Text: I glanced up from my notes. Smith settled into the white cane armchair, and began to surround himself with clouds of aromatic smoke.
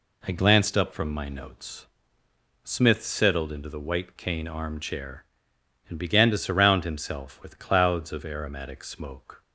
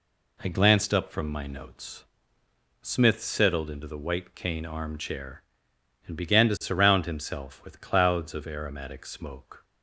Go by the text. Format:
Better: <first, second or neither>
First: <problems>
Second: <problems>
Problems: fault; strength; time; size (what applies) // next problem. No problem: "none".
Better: neither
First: none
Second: none